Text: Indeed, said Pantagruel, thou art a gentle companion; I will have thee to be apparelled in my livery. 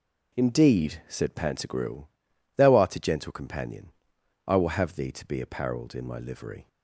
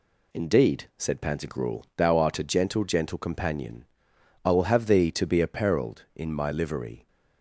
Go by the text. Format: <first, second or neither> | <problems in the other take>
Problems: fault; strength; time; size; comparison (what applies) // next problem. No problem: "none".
first | says "gentle" twice; at 2.8 s